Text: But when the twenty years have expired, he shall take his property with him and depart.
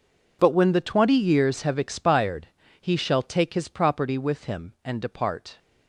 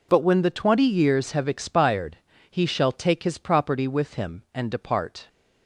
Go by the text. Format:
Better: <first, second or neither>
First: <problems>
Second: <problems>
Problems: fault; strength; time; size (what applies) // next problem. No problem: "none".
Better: second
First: gets quieter; strong; throughout; 17 dB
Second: none